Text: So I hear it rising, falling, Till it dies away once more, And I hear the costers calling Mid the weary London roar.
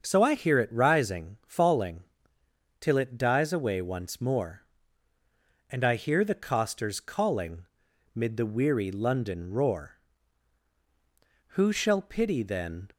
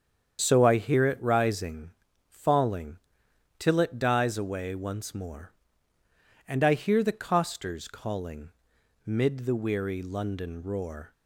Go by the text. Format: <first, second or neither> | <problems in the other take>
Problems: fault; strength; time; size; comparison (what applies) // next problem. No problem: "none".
second | starts louder than the rest; until 1.0 s; 6.5 dB; strong in the second // pauses between "calling" and "Mid"; noticeable; at 7.6 s; 0.48 s long; noticeable in the second // goes on to say "Who shall pity then"; from 11.4 s on; 1.4 s long